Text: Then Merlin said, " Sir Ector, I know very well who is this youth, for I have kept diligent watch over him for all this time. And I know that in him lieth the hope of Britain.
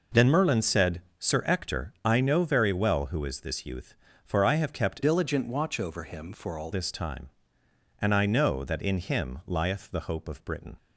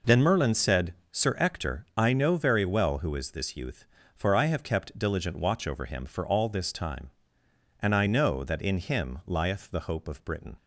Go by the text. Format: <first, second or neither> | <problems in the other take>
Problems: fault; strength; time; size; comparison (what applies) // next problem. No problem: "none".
second | changes voice from "diligent" to "all"; from 5.0 to 6.6 s; 1.6 s long